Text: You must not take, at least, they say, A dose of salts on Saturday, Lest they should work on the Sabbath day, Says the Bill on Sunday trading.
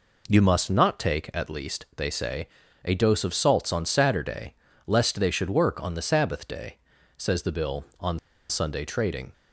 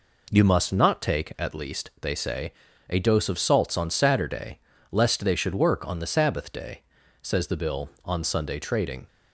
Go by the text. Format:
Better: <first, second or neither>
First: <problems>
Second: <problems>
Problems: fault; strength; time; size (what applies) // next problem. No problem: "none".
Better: second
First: pauses between "on" and "Sunday"; slight; at 8.1 s; 0.31 s long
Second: none